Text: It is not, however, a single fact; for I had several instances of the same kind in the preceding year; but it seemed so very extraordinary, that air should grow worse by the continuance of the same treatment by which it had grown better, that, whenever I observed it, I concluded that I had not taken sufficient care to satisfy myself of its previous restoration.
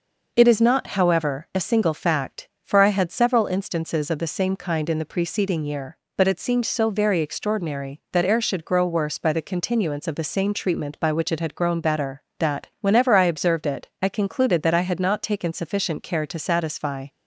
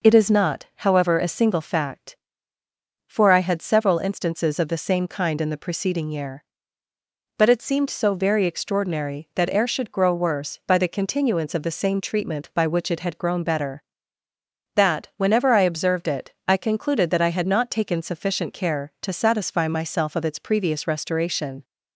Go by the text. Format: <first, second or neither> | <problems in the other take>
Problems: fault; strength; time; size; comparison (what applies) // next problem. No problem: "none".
second | stops before "myself of its previous restoration"; at 17.0 s